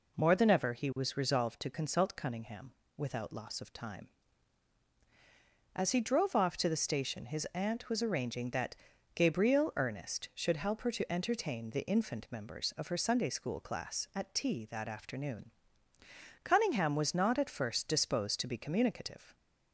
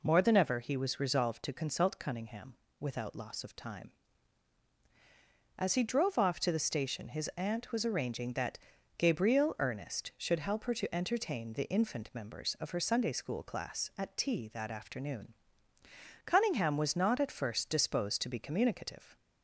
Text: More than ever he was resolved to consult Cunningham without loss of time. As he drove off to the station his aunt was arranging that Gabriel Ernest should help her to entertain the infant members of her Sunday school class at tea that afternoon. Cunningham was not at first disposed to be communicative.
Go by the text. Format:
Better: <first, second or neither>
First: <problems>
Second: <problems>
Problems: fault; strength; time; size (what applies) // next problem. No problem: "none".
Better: neither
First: pauses between "Cunningham" and "without"; slight; at 2.7 s; 0.26 s long // pauses between "that" and "Gabriel"; at 8.7 s; 0.38 s long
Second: pauses between "Cunningham" and "without"; slight; at 2.5 s; 0.26 s long // pauses between "that" and "Gabriel"; at 8.5 s; 0.38 s long